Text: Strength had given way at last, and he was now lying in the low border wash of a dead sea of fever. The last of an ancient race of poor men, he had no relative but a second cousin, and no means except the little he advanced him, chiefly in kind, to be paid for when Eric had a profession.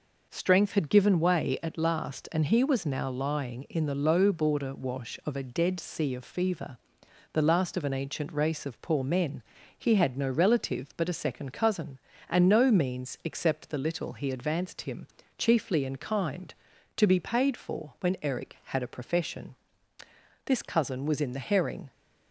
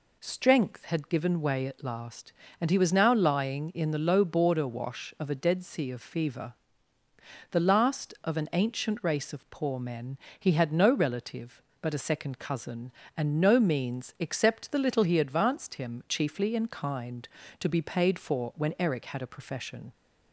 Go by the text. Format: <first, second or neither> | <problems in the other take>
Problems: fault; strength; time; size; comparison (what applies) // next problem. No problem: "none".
second | goes on to say "This cousin was in the herring"; from 20.4 s on; 1.4 s long